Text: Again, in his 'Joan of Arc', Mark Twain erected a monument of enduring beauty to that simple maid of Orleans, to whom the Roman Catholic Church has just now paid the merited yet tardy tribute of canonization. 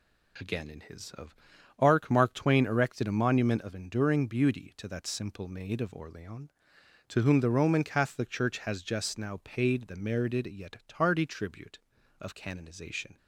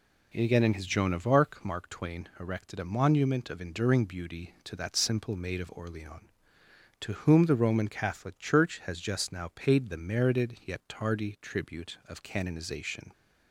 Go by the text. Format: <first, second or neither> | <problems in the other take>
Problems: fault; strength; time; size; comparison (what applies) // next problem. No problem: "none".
second | skips "Joan"; at 1.1 s // pauses between "of" and "Arc"; at 1.3 s; 0.44 s long